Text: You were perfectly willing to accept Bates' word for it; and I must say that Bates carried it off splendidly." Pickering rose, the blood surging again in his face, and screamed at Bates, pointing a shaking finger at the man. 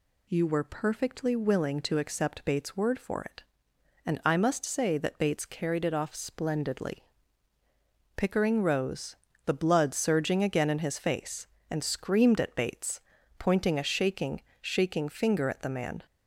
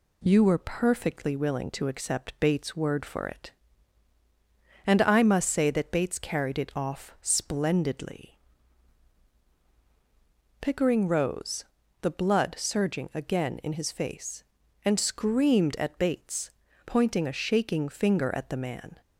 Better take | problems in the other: second | says "shaking" twice; at 14.5 s

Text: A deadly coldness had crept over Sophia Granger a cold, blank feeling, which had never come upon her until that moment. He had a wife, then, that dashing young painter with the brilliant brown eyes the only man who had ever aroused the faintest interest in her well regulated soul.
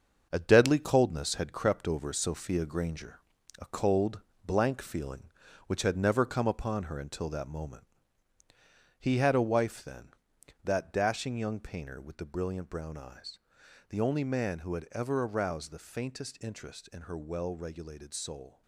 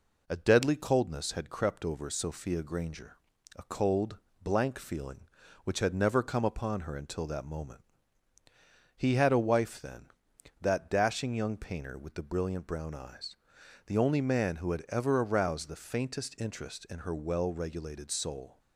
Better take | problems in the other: second | gets quieter; strong; throughout; 7.5 dB // pauses between "Granger" and "a"; at 3.1 s; 0.40 s long; also in the second // pauses between "eyes" and "the"; noticeable; at 13.3 s; 0.50 s long; noticeable in the second

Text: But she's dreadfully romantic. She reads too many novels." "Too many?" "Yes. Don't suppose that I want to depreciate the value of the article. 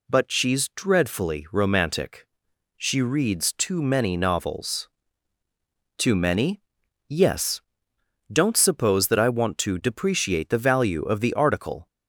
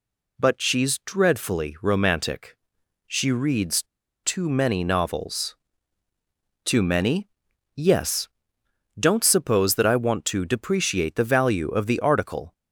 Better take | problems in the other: first | pauses between "reads" and "too"; at 3.8 s; 0.39 s long

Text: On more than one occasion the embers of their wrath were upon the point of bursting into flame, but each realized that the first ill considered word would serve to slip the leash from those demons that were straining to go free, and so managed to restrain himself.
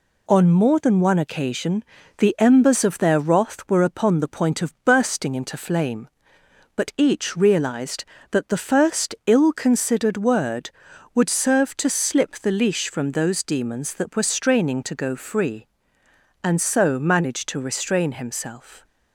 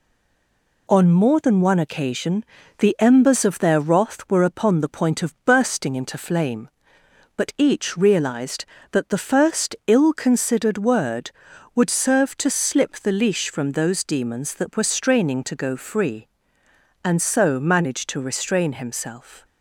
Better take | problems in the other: first | stays silent before the first word; slight; until 0.8 s; 0.8 s long // pauses between "occasion" and "the"; slight; at 2.4 s; 0.34 s long; slight in the first

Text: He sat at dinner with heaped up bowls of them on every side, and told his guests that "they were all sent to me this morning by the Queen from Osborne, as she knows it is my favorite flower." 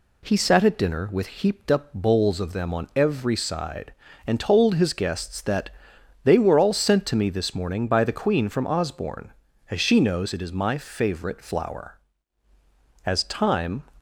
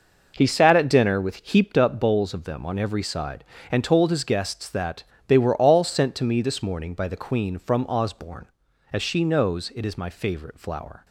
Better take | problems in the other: second | pauses between "that" and "they"; noticeable; at 5.6 s; 0.56 s long; slight in the second // goes on to say "As time"; noticeable; from 13.0 s on; 0.80 s long

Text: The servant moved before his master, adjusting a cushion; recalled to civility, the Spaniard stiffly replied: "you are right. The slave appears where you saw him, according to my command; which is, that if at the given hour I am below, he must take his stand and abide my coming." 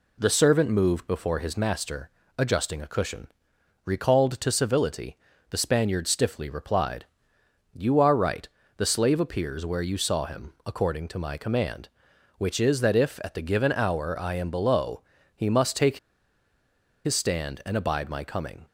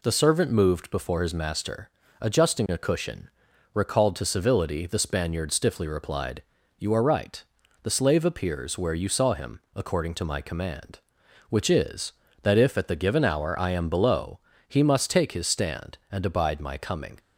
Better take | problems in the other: second | pauses between "take" and "his"; at 15.9 s; 1.0 s long

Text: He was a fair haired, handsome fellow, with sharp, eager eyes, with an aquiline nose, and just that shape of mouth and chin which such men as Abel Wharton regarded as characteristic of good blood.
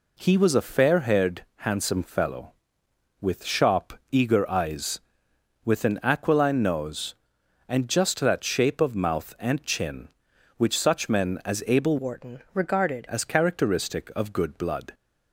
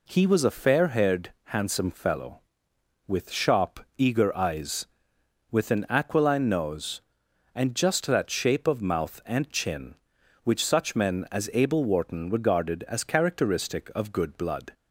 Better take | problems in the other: second | changes voice from "Wharton" to "regarded"; from 11.9 to 13.0 s; 1.1 s long

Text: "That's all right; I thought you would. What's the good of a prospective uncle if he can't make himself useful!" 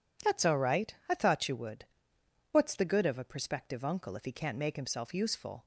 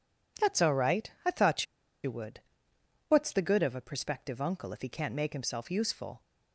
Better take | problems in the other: first | pauses between "thought" and "you"; at 1.6 s; 0.39 s long

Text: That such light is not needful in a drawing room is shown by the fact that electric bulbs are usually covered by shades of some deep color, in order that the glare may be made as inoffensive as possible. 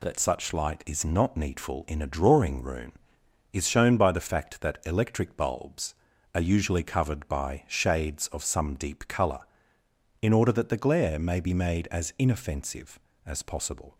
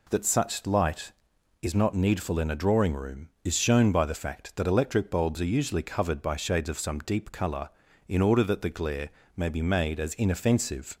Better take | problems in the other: first | pauses between "glare" and "may"; slight; at 9.0 s; 0.26 s long // stops before "as possible"; at 10.9 s

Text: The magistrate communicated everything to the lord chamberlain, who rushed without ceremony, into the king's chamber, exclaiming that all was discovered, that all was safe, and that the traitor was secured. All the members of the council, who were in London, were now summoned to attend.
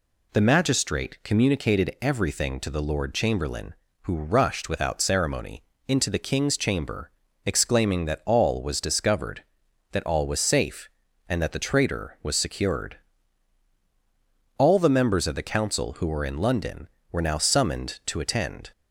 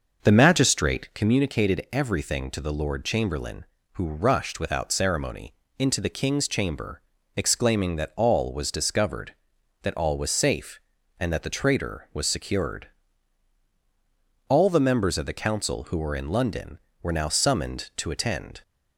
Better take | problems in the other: first | starts louder than the rest; noticeable; until 1.2 s; 6 dB

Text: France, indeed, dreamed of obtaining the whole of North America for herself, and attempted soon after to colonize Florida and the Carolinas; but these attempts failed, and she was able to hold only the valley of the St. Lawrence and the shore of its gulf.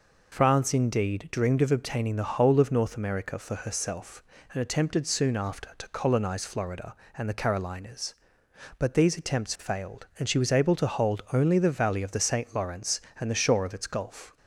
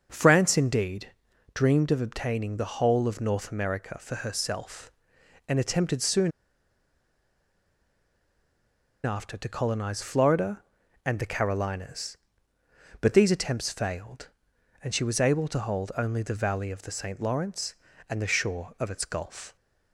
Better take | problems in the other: first | starts louder than the rest; until 1.1 s; 6.5 dB // pauses between "soon" and "after"; strong; at 6.3 s; 2.7 s long

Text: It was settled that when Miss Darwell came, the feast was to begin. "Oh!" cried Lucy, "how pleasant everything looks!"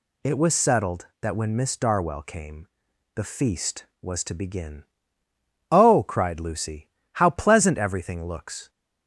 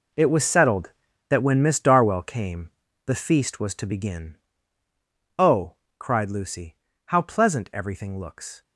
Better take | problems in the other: first | gets quieter; strong; throughout; 13.5 dB

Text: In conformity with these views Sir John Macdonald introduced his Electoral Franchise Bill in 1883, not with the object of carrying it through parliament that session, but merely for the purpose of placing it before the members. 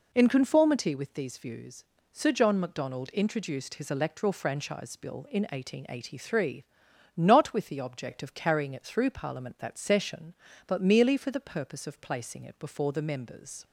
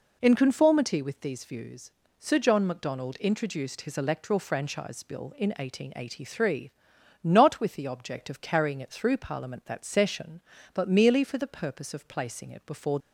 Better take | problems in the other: first | pauses between "views" and "Sir"; slight; at 1.9 s; 0.28 s long; slight in the first // stops before "the members"; at 12.9 s

